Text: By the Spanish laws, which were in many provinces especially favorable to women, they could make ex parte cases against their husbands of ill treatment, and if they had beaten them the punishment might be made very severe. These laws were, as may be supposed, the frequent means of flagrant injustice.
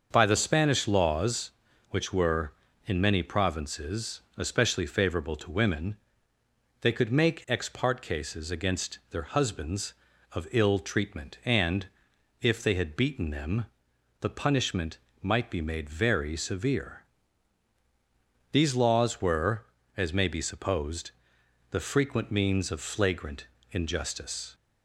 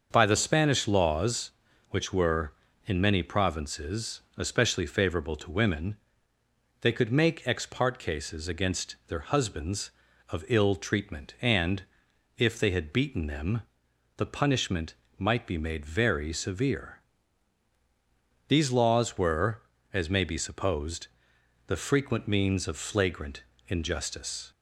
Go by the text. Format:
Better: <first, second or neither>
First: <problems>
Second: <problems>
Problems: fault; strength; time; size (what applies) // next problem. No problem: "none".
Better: neither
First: starts louder than the rest; until 1.1 s; 6.5 dB // pauses between "provinces" and "especially"; slight; at 4.1 s; 0.16 s long // pauses between "and" and "if"; noticeable; at 11.8 s; 0.54 s long // pauses between "them" and "the"; noticeable; at 13.6 s; 0.56 s long // pauses between "punishment" and "might"; slight; at 14.9 s; 0.22 s long // pauses between "flagrant" and "injustice"; slight; at 23.4 s; 0.26 s long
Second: starts louder than the rest; until 1.1 s; 6.5 dB // pauses between "provinces" and "especially"; slight; at 4.1 s; 0.16 s long // pauses between "and" and "if"; noticeable; at 11.8 s; 0.54 s long // pauses between "them" and "the"; noticeable; at 13.6 s; 0.56 s long // pauses between "punishment" and "might"; slight; at 14.9 s; 0.22 s long // pauses between "flagrant" and "injustice"; slight; at 23.4 s; 0.26 s long